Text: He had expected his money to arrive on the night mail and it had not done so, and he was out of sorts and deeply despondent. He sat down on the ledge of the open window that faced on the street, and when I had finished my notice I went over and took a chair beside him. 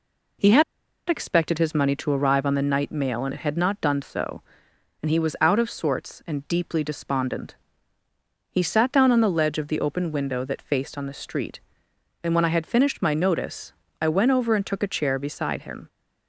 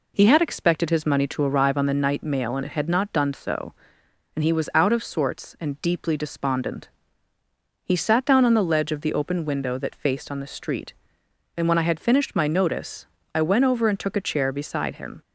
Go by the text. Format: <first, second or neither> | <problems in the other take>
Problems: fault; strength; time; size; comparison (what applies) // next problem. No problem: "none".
second | pauses between "had" and "expected"; at 0.6 s; 0.45 s long // pauses between "notice" and "I"; slight; at 13.7 s; 0.30 s long; slight in the second